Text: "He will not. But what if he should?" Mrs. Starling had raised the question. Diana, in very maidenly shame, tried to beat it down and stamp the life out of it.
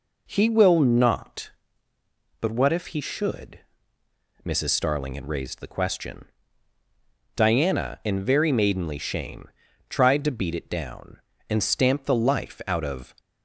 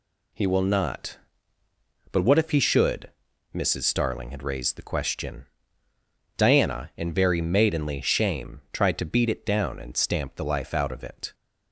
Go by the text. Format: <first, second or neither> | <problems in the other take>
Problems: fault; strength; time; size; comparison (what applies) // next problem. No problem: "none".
second | stops before "it"; at 13.1 s